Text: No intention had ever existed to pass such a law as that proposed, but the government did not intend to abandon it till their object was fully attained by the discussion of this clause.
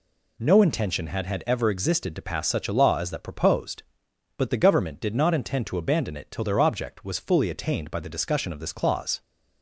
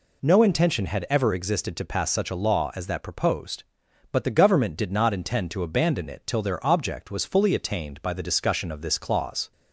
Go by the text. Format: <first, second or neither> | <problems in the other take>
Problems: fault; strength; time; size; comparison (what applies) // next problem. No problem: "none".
second | says "had" twice; at 1.2 s